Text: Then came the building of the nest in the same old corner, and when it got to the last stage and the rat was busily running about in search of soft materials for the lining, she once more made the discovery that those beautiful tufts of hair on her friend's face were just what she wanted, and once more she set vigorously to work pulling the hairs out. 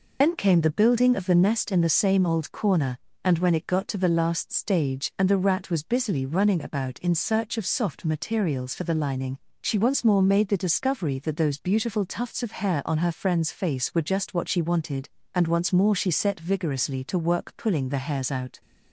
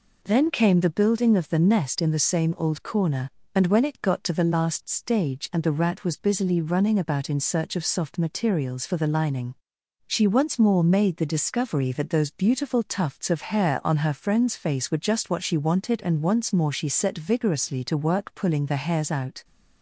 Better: second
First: loses the start of "Then"; at 0.2 s; 140 ms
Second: none

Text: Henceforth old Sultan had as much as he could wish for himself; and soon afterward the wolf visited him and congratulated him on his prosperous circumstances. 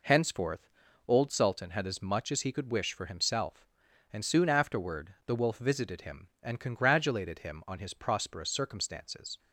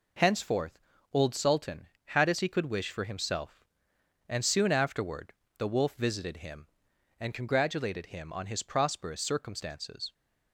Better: first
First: pauses between "Henceforth" and "old"; at 0.6 s; 0.38 s long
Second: pauses between "Henceforth" and "old"; slight; at 0.7 s; 0.34 s long // skips "much as"; at 2.4 s // pauses between "afterward" and "the"; slight; at 5.3 s; 0.24 s long

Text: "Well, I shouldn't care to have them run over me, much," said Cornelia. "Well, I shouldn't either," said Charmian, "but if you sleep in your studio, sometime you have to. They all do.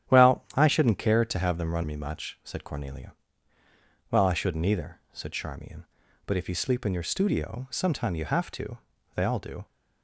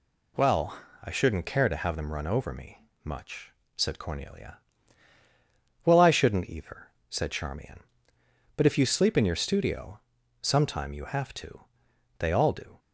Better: second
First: starts louder than the rest; strong; until 1.1 s; 10 dB // skips "over"; at 1.8 s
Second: none

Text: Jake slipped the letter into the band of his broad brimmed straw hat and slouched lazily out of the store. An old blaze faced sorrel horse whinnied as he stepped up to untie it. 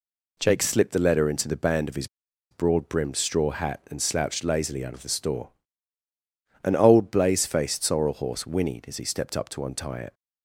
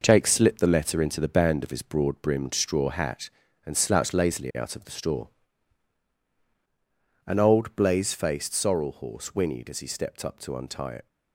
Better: second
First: pauses between "his" and "broad"; at 2.0 s; 0.43 s long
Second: none

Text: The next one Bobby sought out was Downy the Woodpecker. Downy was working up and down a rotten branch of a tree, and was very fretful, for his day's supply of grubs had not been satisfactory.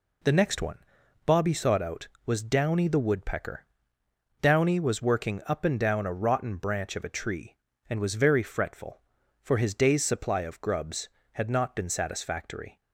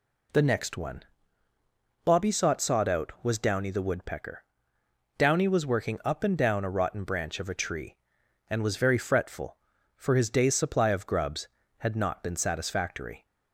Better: first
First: pauses between "one" and "Bobby"; noticeable; at 0.7 s; 0.46 s long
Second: pauses between "one" and "Bobby"; at 1.0 s; 1.0 s long // says "sought" twice; at 2.6 s

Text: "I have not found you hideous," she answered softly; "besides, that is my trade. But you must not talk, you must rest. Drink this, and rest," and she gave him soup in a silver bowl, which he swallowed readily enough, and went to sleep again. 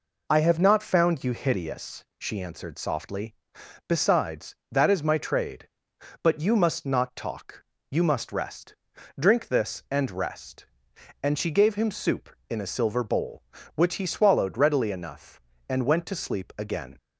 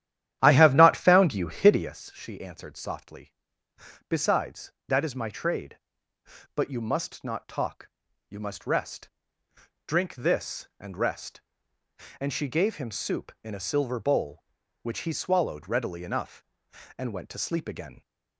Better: first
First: none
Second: starts louder than the rest; strong; until 2.0 s; 11.5 dB

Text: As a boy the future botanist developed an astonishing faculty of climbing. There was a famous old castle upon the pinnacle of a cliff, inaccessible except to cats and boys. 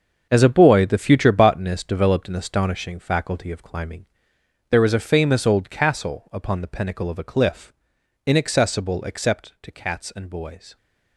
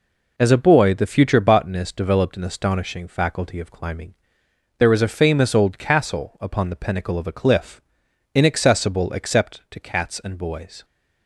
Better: second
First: gets quieter; strong; throughout; 11 dB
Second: none

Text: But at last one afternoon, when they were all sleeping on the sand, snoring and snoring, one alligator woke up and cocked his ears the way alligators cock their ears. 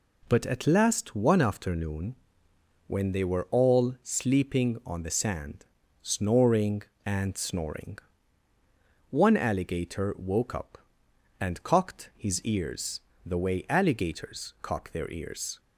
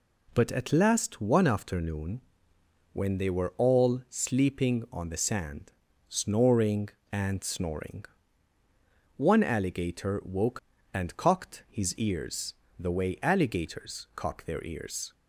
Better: first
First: pauses between "ears" and "the"; slight; at 13.0 s; 0.24 s long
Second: skips "up"; at 10.7 s // pauses between "ears" and "the"; slight; at 12.5 s; 0.24 s long

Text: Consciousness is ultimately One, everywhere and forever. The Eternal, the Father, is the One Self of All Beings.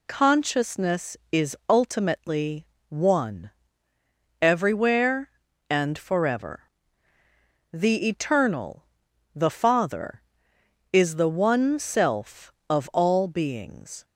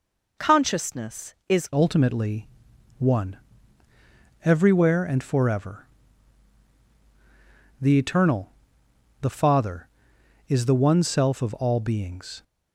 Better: first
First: pauses between "ultimately" and "One"; slight; at 2.6 s; 0.24 s long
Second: changes voice at "ultimately"; from 1.7 s on; 10.7 s long // pauses between "ultimately" and "One"; noticeable; at 2.4 s; 0.54 s long

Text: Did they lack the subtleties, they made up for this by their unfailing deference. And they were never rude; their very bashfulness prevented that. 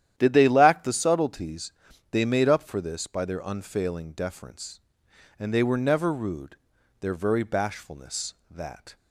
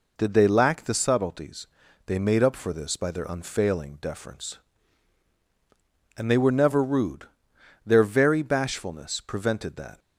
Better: second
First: starts louder than the rest; strong; until 1.1 s; 11 dB // skips "prevented"; at 8.4 s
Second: none

